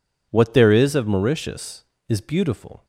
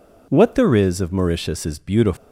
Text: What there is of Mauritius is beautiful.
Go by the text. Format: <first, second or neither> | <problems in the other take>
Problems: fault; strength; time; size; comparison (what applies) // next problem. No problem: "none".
neither | none